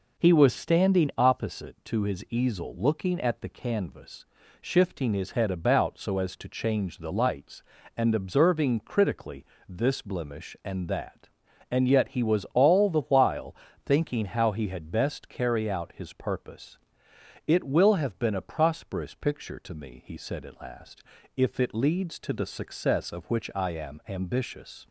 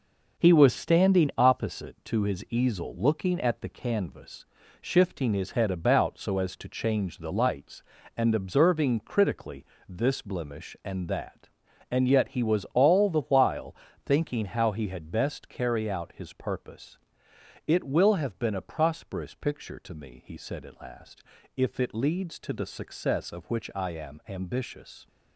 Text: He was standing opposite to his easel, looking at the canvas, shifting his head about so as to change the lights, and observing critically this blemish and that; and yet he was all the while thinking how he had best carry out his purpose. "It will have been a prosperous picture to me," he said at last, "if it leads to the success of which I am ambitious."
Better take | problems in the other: first | gets quieter; throughout; 7 dB // pauses between "critically" and "this"; slight; at 9.6 s; 0.24 s long; slight in the first // pauses between "while" and "thinking"; slight; at 13.7 s; 0.30 s long; slight in the first

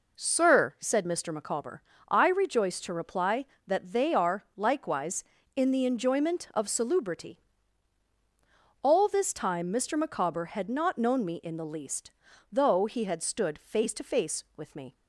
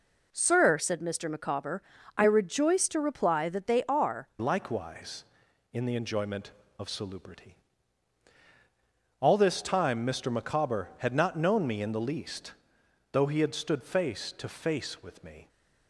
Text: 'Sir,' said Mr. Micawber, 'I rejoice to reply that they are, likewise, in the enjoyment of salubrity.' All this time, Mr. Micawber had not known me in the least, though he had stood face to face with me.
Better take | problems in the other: first | changes voice at "likewise"; from 4.3 s on; 11.1 s long

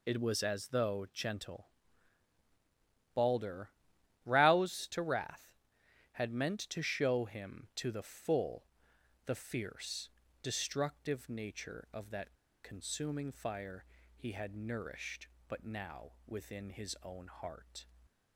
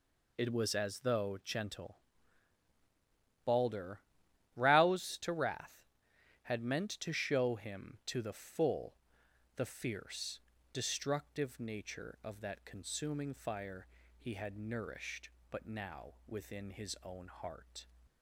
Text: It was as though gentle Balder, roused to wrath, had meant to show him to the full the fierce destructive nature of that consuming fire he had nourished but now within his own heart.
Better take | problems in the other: second | pauses between "gentle" and "Balder"; strong; at 1.6 s; 1.4 s long; strong in the second // pauses between "full" and "the"; noticeable; at 8.6 s; 0.62 s long; noticeable in the second // pauses between "fierce" and "destructive"; slight; at 10.0 s; 0.34 s long; slight in the second // pauses between "that" and "consuming"; slight; at 12.3 s; 0.30 s long // pauses between "fire" and "he"; slight; at 13.8 s; 0.30 s long; slight in the second

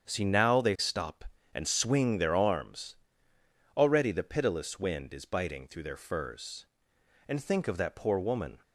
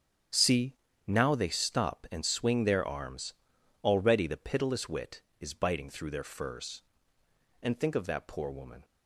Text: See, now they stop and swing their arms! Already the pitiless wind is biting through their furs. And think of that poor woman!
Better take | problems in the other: first | starts louder than the rest; strong; until 1.6 s; 8.5 dB; strong in the first // says "wit" for "wind"; at 4.8 s

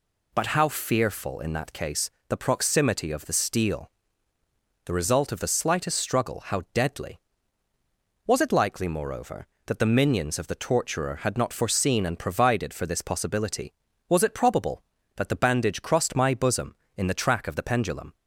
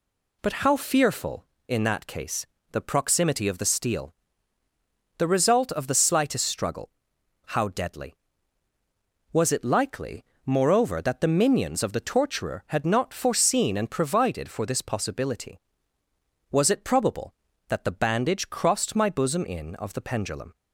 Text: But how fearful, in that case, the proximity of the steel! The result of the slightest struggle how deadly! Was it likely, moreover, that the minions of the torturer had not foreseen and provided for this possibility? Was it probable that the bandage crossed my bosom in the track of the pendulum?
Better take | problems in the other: first | pauses between "struggle" and "how"; noticeable; at 6.8 s; 0.62 s long // skips "the track"; at 19.7 s

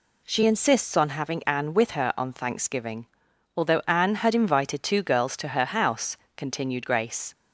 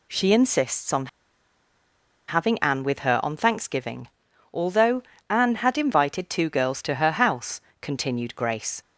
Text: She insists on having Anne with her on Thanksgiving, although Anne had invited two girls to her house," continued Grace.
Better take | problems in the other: first | pauses between "on" and "having"; at 1.0 s; 1.2 s long // pauses between "although" and "Anne"; slight; at 5.0 s; 0.26 s long

